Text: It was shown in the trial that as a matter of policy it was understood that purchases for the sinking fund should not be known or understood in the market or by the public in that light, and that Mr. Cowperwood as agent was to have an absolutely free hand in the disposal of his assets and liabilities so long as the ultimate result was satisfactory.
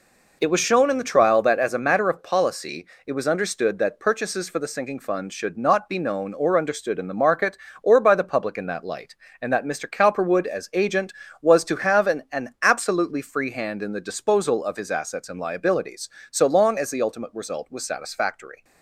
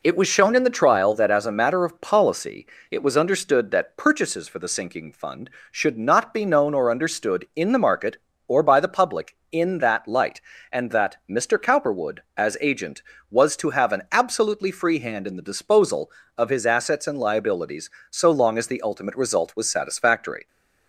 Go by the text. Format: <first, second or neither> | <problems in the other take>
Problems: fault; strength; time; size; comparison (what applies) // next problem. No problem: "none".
second | pauses between "policy" and "it"; slight; at 2.8 s; 0.20 s long; slight in the second // says "an" twice; at 12.3 s